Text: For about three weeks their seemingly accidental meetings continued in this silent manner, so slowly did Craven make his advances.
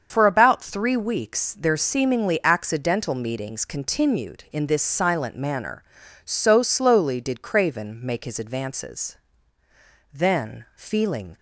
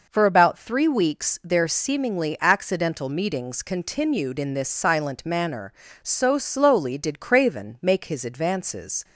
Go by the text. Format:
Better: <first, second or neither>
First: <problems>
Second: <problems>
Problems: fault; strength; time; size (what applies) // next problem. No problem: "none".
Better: second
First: starts louder than the rest; until 1.1 s; 7 dB // goes on to say "Then feeling"; noticeable; from 10.1 s on; 1.2 s long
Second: none